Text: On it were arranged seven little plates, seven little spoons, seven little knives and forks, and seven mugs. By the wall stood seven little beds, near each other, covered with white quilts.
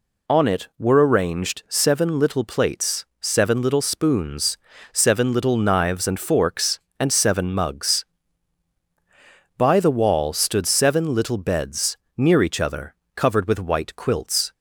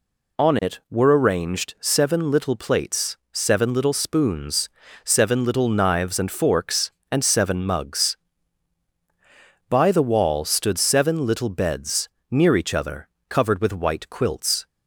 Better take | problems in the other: neither | none

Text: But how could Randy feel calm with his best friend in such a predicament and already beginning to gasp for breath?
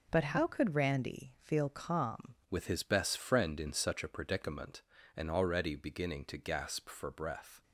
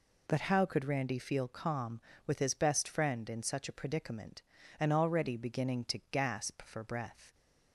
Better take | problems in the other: second | changes voice at "with"; from 2.5 s on; 5.1 s long

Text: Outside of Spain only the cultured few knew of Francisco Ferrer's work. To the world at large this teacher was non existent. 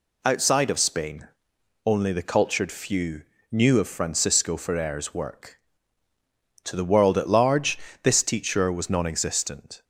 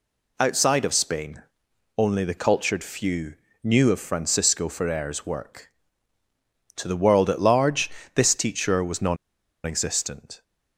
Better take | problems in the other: first | pauses between "Spain" and "only"; noticeable; at 1.4 s; 0.54 s long; noticeable in the first // pauses between "few" and "knew"; slight; at 3.3 s; 0.28 s long; slight in the first // pauses between "large" and "this"; slight; at 7.8 s; 0.26 s long; slight in the first // pauses between "non" and "existent"; noticeable; at 9.1 s; 0.48 s long

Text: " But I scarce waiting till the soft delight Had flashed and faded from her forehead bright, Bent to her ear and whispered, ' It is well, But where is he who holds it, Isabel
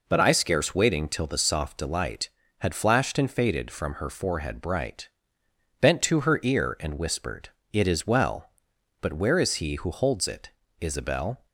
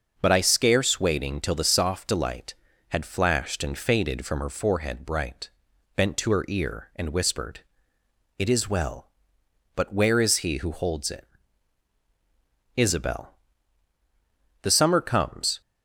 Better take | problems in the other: first | starts louder than the rest; until 1.1 s; 7 dB // goes on to say "The summer comes"; noticeable; from 14.6 s on; 0.98 s long

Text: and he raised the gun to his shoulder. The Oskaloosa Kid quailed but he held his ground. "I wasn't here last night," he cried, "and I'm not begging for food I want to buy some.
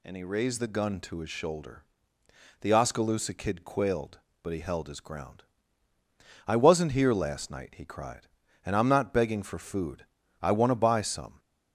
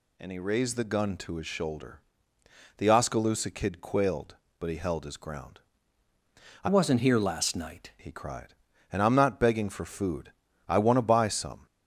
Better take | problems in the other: first | changes voice from "wasn't" to "night"; from 6.6 to 7.9 s; 1.3 s long // pauses between "food" and "I"; slight; at 10.3 s; 0.34 s long; slight in the first

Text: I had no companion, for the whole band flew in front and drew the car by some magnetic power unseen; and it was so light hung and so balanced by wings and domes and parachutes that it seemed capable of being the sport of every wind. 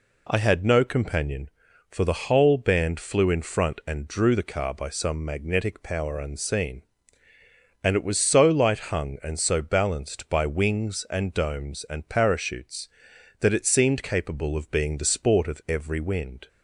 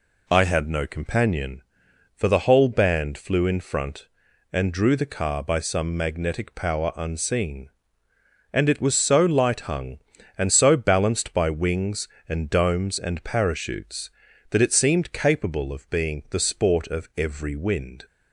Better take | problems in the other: neither | none

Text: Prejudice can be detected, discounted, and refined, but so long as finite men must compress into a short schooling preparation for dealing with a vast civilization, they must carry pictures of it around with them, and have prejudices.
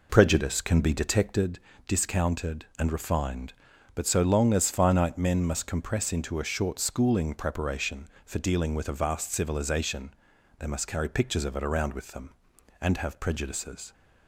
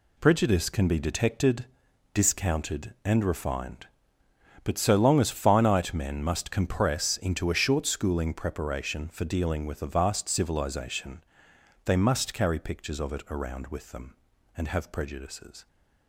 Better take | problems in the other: second | starts louder than the rest; noticeable; until 1.4 s; 4 dB

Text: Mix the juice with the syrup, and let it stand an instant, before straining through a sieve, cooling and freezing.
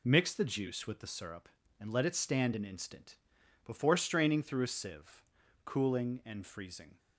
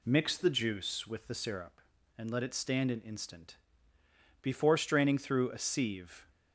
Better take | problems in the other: first | stops before "cooling and freezing"; at 6.2 s

